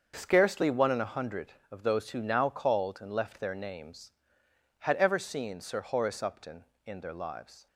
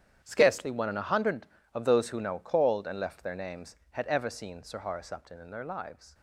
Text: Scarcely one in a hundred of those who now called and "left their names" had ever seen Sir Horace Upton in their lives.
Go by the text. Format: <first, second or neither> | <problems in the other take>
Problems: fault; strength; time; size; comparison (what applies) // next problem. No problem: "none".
first | gets quieter; strong; throughout; 13 dB // starts louder than the rest; strong; until 1.2 s; 10 dB; also in the first